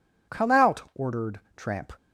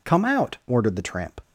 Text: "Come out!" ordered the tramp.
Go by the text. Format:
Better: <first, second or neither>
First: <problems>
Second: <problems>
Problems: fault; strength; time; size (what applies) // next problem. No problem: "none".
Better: second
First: skips "the"; at 1.4 s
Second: none